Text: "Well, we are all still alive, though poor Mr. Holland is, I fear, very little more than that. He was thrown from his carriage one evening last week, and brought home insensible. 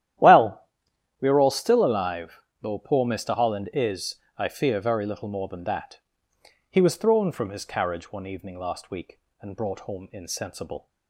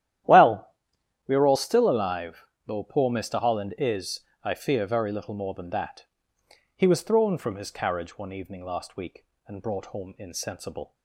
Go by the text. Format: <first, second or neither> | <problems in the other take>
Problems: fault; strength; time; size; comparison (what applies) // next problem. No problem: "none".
neither | starts louder than the rest; strong; the same in both